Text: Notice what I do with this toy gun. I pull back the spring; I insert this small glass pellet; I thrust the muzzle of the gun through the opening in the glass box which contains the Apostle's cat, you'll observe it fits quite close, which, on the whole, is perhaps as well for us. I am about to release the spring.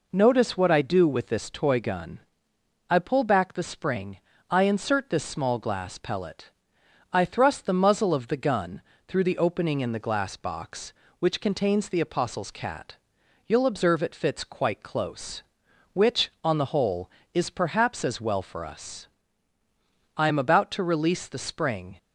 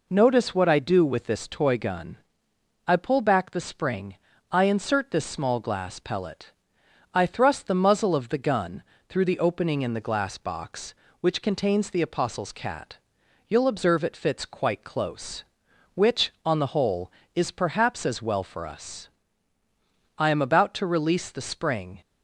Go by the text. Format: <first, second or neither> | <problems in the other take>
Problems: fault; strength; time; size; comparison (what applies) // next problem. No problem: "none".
neither | pauses between "gun" and "through"; slight; the same in both